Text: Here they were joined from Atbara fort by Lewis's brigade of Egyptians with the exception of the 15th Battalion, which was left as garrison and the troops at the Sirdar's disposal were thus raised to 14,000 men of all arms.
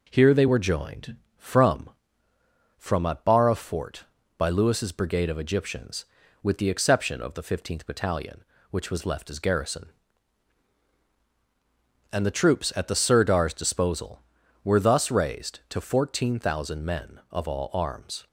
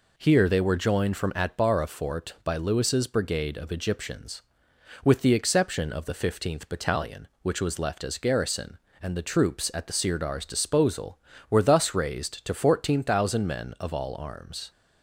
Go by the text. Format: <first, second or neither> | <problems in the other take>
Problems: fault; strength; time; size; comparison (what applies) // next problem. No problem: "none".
second | says "from" twice; at 2.7 s